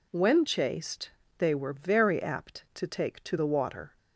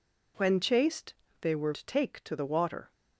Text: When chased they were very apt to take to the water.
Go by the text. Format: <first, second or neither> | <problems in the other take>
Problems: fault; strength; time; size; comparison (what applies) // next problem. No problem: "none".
first | pauses between "chased" and "they"; slight; at 1.1 s; 0.26 s long; slight in the first // skips "very apt"; at 1.7 s